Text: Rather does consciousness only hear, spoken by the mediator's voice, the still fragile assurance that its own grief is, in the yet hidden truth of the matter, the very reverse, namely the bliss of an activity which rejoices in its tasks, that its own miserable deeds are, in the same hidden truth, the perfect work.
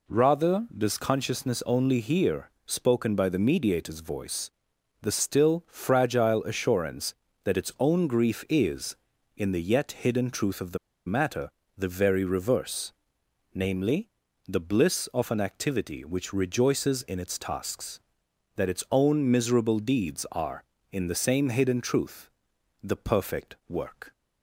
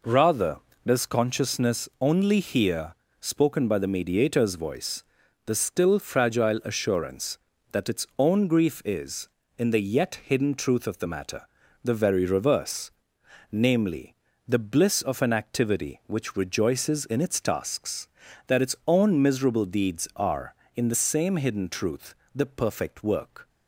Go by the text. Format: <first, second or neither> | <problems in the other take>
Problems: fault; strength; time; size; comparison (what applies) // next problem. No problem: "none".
second | pauses between "the" and "matter"; slight; at 10.7 s; 0.28 s long // pauses between "namely" and "the"; at 14.0 s; 0.40 s long; slight in the second